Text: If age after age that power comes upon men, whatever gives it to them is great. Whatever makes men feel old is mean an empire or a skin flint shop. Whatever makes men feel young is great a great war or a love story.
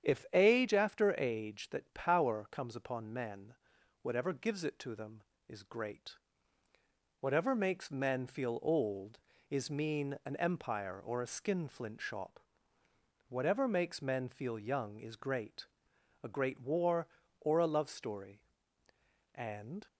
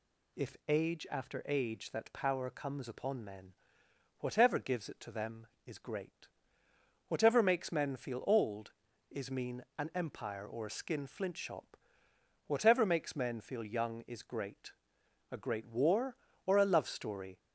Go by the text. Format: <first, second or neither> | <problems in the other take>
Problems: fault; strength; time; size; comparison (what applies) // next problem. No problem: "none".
second | starts louder than the rest; strong; until 1.1 s; 8.5 dB // pauses between "great" and "a"; noticeable; at 15.6 s; 0.54 s long; noticeable in the second // goes on to say "And"; from 19.3 s on; 0.50 s long